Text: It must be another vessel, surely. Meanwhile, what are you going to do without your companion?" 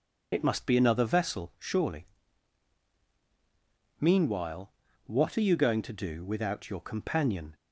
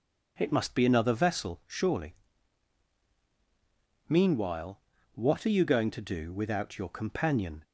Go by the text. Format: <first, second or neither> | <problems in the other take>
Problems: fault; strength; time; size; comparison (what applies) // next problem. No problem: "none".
second | loses the start of "It"; at 0.3 s; 40 ms